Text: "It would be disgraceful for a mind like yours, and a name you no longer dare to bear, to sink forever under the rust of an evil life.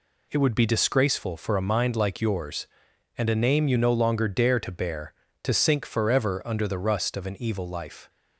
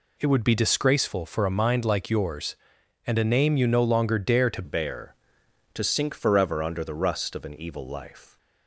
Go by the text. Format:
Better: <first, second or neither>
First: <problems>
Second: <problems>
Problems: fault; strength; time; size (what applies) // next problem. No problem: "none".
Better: first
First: none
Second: changes voice at "bear"; from 4.6 s on; 3.7 s long